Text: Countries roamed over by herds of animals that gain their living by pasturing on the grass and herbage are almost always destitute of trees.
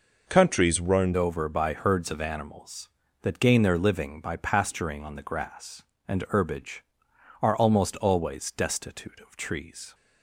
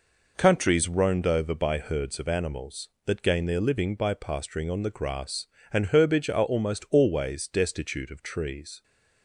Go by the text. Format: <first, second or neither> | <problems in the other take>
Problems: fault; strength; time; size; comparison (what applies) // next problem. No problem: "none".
second | changes voice at "over"; from 1.1 s on; 8.8 s long